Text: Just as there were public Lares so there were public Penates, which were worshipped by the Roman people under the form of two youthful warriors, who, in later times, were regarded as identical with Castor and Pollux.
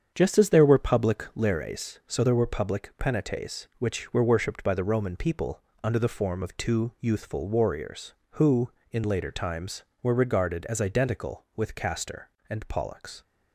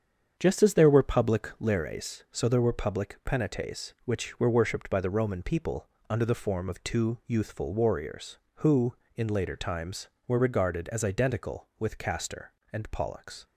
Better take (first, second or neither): neither